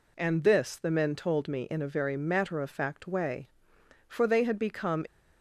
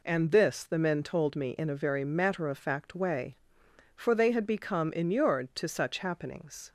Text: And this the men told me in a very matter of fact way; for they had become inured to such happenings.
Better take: second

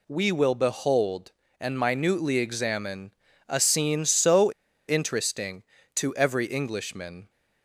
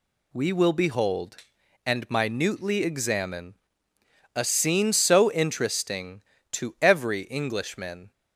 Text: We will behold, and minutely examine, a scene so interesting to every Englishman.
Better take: second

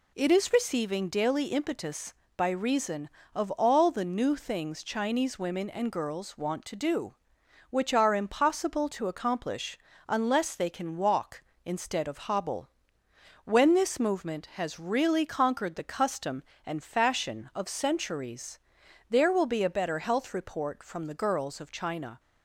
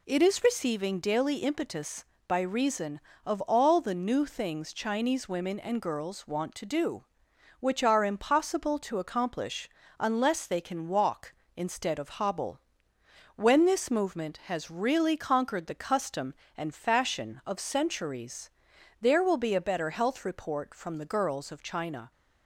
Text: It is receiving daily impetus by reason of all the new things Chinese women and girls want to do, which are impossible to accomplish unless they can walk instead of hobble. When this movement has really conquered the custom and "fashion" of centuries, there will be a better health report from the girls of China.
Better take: neither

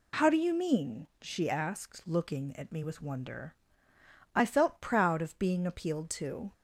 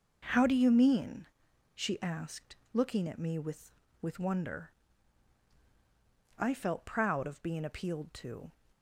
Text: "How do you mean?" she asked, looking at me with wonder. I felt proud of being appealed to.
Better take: first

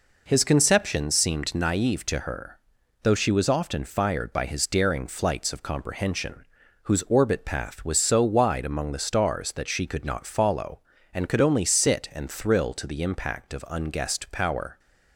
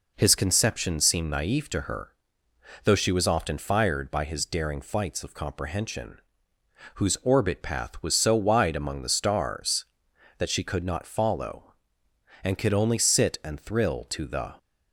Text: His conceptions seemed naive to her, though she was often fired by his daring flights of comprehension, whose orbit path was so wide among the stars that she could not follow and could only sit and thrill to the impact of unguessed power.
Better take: first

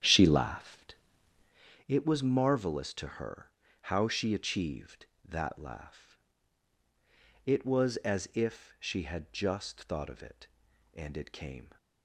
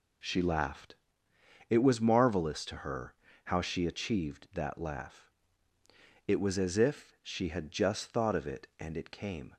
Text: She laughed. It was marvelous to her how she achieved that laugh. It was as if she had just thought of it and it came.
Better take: second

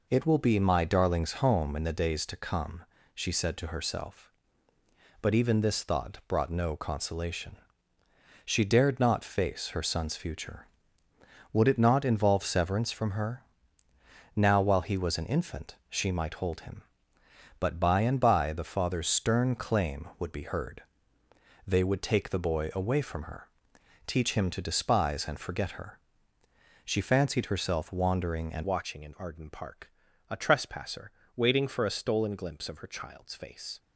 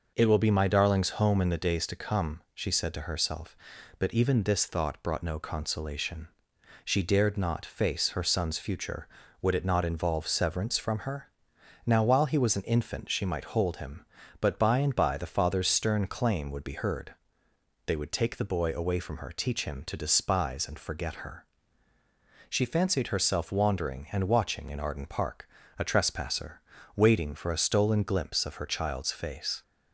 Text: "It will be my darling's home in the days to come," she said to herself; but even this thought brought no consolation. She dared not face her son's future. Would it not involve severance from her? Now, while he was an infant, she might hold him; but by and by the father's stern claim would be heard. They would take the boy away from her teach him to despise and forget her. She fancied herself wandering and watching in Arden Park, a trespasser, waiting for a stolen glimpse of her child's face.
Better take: second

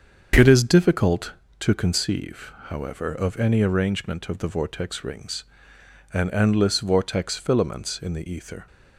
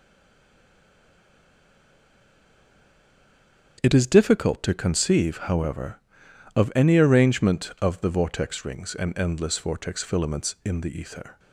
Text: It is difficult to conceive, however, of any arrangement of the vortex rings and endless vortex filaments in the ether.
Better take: first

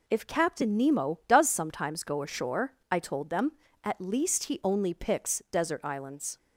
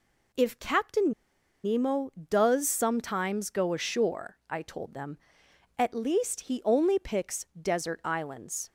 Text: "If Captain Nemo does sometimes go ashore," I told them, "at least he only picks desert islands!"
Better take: first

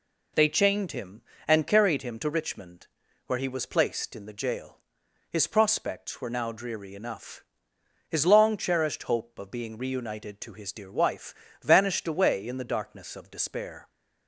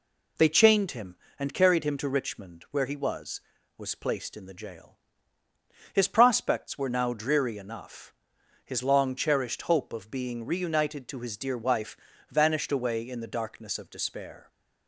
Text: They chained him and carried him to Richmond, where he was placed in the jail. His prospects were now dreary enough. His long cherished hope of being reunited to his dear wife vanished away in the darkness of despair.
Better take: first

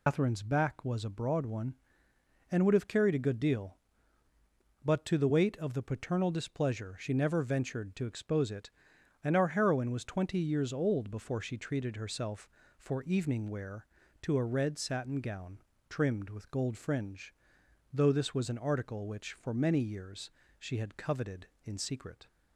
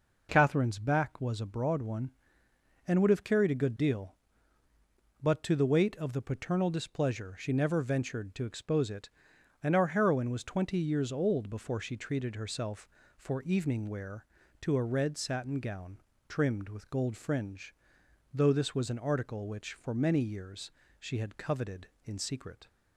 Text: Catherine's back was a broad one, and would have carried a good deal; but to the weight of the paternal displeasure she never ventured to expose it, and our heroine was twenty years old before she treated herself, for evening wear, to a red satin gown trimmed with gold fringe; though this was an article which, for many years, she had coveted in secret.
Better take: second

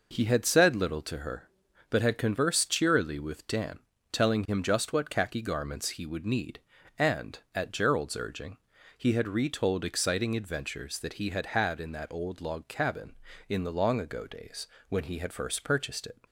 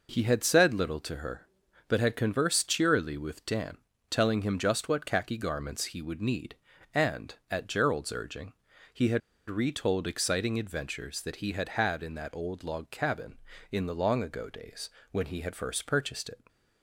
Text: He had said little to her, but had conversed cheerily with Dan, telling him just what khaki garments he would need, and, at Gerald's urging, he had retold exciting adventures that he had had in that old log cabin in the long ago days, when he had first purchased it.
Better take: first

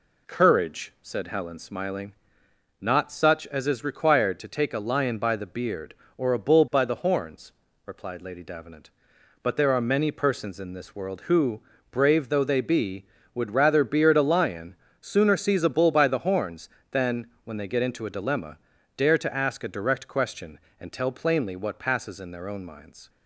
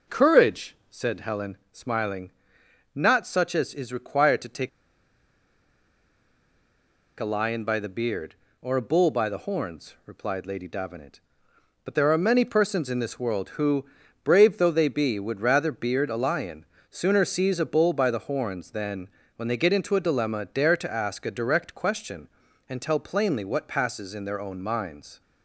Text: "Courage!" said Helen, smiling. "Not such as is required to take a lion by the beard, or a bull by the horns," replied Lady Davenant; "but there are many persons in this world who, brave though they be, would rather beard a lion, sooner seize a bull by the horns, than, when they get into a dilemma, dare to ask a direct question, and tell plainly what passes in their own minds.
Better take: first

